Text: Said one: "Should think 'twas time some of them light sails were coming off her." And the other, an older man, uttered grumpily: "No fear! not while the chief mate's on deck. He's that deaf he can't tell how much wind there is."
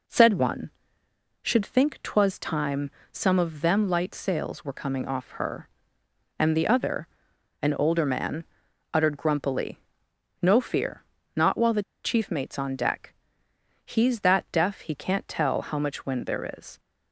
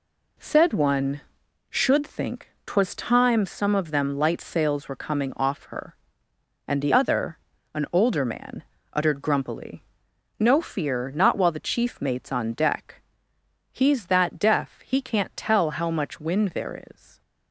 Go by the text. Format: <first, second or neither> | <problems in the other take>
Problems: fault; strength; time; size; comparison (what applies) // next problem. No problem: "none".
second | pauses between "time" and "some"; slight; at 2.8 s; 0.24 s long // pauses between "the" and "chief"; slight; at 11.8 s; 0.22 s long